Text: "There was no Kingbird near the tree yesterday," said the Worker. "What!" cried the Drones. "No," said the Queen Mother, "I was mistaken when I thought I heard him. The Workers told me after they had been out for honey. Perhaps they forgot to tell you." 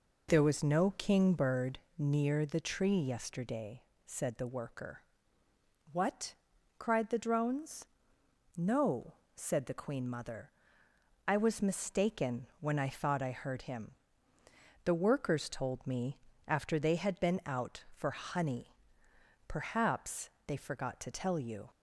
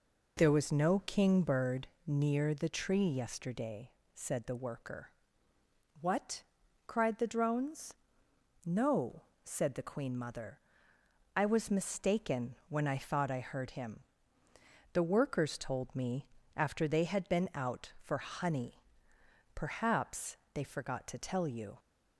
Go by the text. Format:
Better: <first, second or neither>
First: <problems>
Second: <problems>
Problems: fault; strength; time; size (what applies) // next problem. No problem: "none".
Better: neither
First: pauses between "Kingbird" and "near"; slight; at 1.7 s; 0.18 s long // pauses between "me" and "after"; slight; at 16.1 s; 0.28 s long // pauses between "Perhaps" and "they"; slight; at 20.2 s; 0.16 s long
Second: pauses between "Kingbird" and "near"; slight; at 1.8 s; 0.18 s long // pauses between "me" and "after"; slight; at 16.2 s; 0.28 s long // pauses between "Perhaps" and "they"; slight; at 20.3 s; 0.16 s long